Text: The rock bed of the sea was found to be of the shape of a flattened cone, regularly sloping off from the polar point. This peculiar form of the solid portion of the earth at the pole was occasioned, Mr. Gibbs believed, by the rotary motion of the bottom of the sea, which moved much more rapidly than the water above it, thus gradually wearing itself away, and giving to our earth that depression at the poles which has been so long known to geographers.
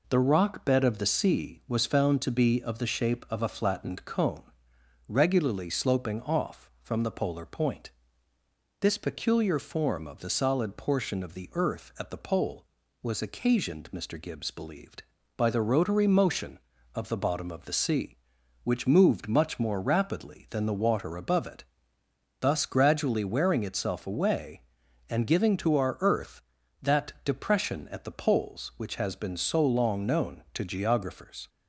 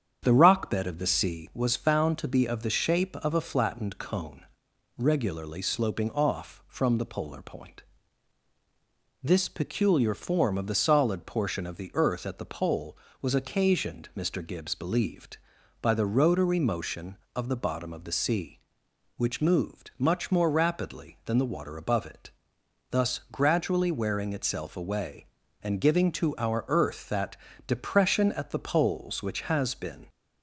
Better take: first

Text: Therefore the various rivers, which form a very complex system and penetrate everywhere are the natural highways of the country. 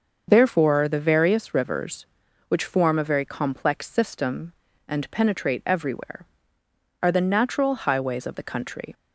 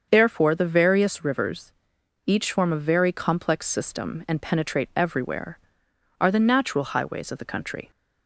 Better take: first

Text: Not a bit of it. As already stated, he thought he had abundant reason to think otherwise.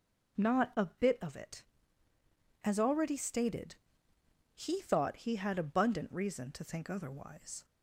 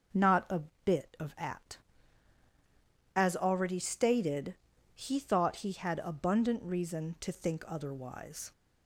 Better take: first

